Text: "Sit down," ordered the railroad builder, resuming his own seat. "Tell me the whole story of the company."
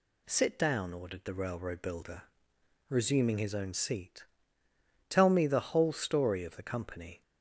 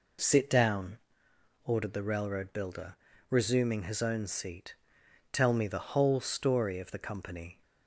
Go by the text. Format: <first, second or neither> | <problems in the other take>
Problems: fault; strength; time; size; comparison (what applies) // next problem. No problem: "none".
neither | none